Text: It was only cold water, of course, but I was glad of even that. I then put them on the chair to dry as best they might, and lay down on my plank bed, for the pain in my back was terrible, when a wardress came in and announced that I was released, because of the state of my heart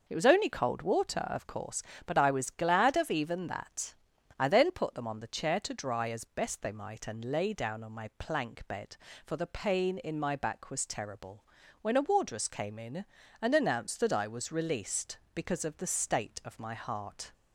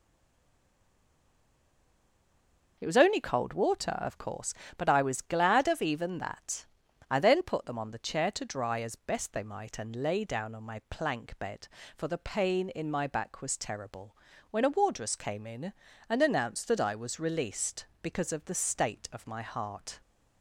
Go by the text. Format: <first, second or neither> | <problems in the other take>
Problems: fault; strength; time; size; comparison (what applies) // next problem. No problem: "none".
first | stays silent before the first word; strong; until 2.7 s; 2.7 s long